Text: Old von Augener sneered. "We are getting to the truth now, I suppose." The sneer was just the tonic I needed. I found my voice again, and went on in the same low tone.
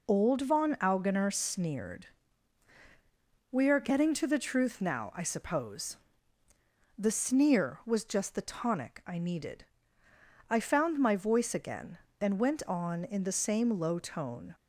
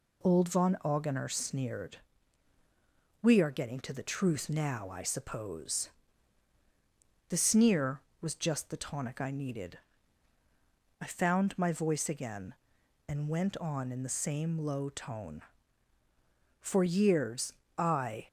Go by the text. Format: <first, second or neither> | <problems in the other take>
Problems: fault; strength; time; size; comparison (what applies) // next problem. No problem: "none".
first | goes on to say "For years I"; strong; from 16.5 s on; 1.6 s long